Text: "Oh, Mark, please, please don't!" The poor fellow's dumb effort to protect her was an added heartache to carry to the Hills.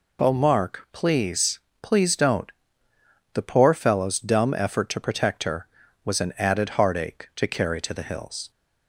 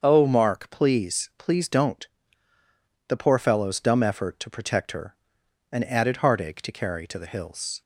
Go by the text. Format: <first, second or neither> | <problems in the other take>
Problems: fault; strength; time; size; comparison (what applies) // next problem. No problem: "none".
first | starts louder than the rest; until 1.0 s; 7 dB // skips "was"; at 5.4 s